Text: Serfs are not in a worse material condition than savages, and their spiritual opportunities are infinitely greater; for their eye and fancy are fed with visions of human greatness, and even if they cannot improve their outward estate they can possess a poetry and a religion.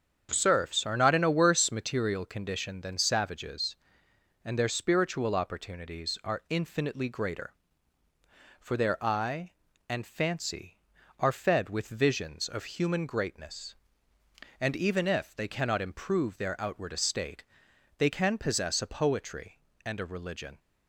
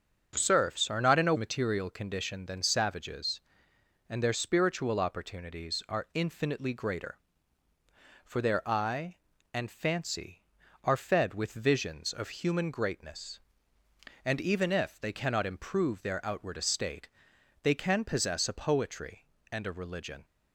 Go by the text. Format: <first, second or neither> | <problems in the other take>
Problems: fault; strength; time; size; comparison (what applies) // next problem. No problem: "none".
first | starts louder than the rest; until 1.4 s; 7 dB; strong in the first // skips "worse"; at 1.3 s // pauses between "estate" and "they"; noticeable; at 17.0 s; 0.56 s long; noticeable in the first